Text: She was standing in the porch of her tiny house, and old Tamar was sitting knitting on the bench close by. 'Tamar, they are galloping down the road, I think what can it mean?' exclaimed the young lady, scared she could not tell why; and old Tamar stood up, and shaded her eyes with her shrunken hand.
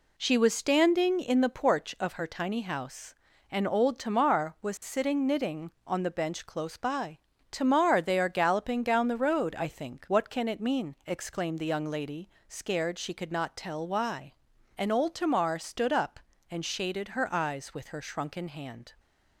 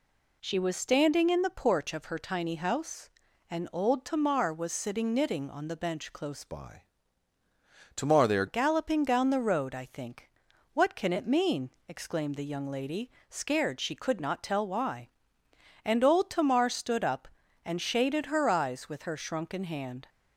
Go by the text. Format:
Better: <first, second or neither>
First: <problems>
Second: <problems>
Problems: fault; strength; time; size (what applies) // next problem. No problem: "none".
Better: first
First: none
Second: changes voice from "by" to "are"; from 6.4 to 8.4 s; 2.0 s long // pauses between "think" and "what"; noticeable; at 10.2 s; 0.46 s long